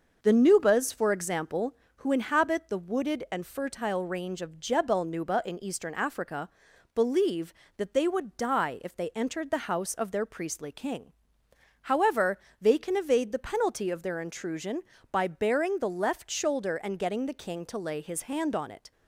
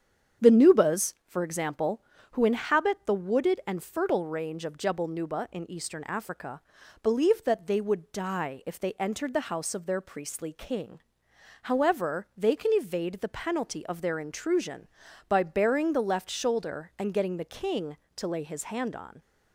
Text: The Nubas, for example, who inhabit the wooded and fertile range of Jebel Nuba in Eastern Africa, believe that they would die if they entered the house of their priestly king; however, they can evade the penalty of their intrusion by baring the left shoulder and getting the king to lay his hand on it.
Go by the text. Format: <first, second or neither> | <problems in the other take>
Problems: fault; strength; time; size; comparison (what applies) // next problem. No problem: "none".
first | starts louder than the rest; strong; until 1.5 s; 8 dB; also in the first // stops before "it"; at 19.2 s